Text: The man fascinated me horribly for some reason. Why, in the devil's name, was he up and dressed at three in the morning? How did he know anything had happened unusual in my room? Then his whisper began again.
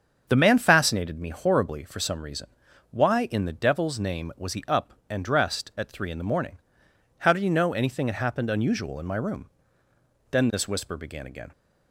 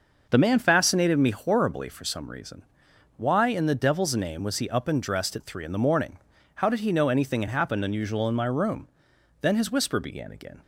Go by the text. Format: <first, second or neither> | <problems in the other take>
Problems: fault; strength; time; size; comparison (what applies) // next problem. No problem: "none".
second | starts louder than the rest; strong; until 1.2 s; 7 dB // says "this" for "his"; at 10.5 s